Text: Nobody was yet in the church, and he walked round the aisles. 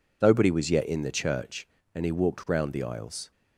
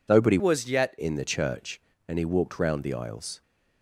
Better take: first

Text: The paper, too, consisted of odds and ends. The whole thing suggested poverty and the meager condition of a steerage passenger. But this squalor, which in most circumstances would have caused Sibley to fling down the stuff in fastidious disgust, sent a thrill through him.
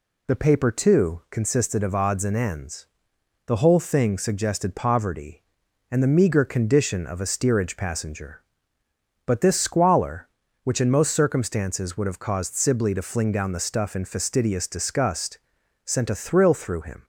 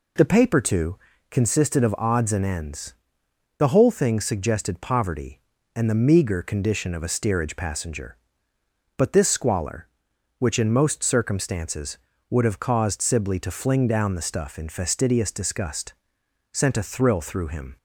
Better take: neither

